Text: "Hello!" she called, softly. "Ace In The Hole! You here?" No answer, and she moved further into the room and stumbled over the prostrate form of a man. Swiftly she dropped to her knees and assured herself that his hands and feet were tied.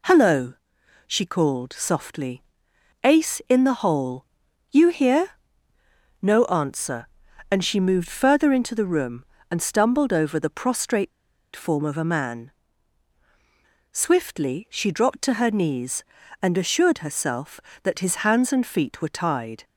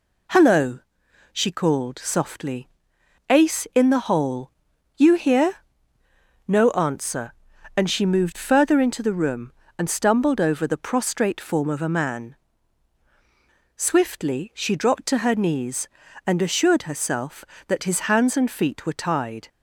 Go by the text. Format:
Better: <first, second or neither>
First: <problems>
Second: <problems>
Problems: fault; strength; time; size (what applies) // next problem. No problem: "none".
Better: second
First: pauses between "prostrate" and "form"; at 11.1 s; 0.45 s long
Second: none